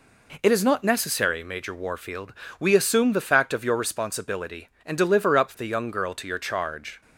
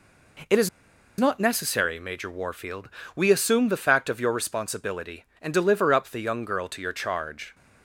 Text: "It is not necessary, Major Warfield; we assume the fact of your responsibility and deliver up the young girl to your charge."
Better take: first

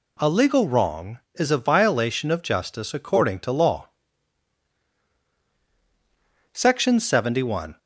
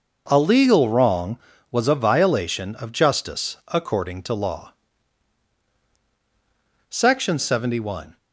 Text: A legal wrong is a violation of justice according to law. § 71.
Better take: first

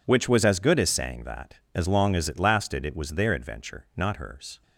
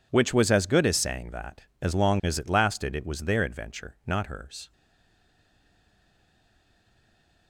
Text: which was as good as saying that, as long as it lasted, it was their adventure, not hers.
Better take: first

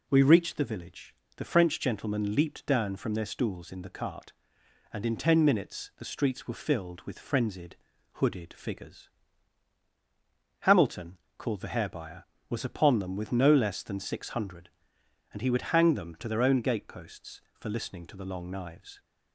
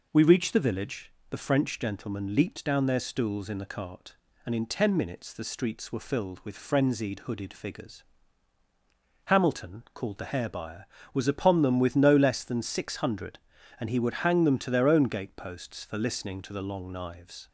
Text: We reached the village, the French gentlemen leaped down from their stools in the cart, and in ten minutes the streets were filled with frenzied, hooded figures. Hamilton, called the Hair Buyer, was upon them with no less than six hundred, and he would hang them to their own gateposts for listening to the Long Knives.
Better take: first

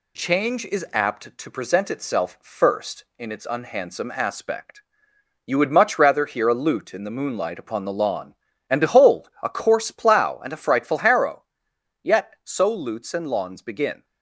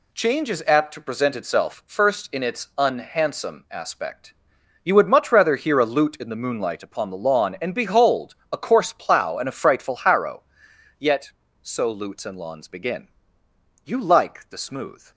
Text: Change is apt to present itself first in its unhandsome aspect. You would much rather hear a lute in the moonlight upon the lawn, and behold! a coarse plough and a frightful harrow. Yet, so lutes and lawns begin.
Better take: first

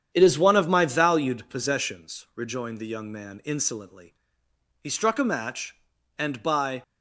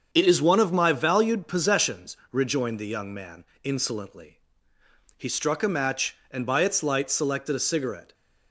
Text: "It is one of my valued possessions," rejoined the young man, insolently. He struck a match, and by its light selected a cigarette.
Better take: second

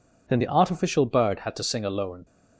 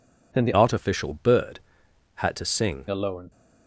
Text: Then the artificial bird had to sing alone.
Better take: first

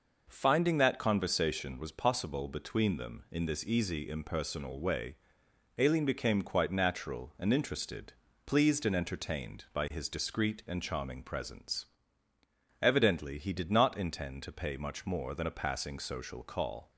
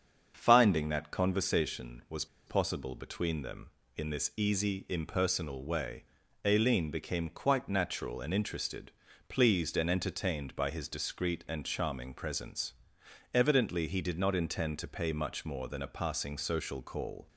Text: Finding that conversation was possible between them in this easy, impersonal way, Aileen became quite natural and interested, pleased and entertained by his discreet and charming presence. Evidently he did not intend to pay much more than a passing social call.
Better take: first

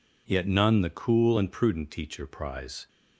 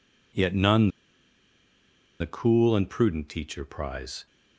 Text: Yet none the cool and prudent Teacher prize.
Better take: first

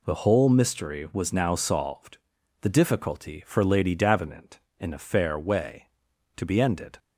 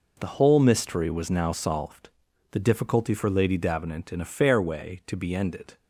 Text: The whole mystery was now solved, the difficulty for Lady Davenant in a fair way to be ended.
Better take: neither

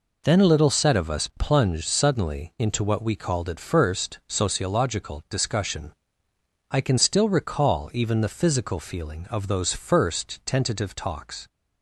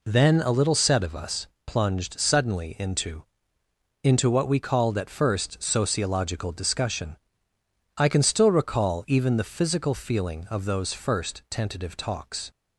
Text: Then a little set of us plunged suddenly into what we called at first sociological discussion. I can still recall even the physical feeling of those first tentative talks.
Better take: first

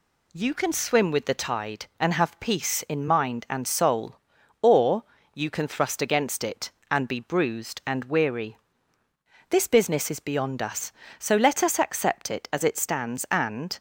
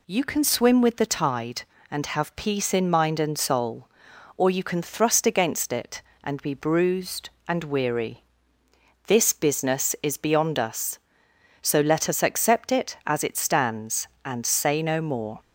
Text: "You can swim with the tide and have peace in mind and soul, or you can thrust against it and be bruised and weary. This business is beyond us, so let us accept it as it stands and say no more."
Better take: second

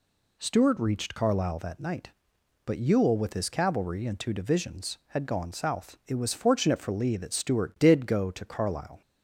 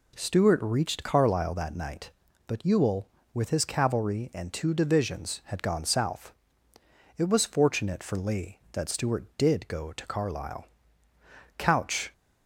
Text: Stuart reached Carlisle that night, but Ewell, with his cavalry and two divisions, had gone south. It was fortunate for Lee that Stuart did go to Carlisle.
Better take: first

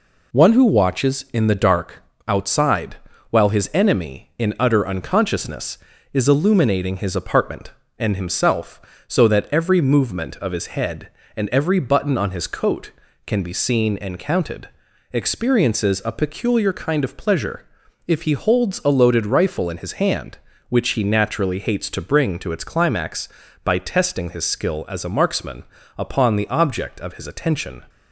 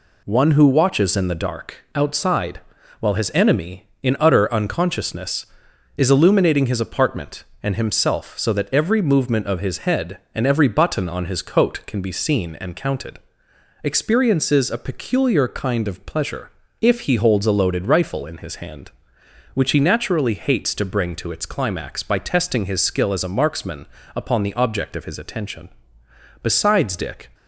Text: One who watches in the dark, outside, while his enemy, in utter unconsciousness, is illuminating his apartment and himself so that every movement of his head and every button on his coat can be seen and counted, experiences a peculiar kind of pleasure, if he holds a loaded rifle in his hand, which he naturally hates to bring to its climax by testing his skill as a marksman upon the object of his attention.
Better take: first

